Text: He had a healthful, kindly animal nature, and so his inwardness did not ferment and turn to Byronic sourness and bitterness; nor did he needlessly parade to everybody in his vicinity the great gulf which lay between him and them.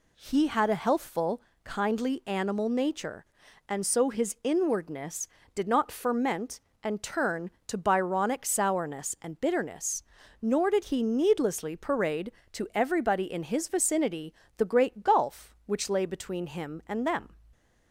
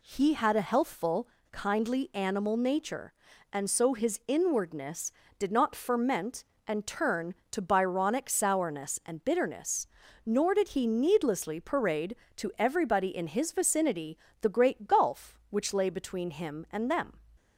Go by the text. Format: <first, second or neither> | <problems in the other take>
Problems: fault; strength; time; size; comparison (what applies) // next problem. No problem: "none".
neither | pauses between "vicinity" and "the"; slight; the same in both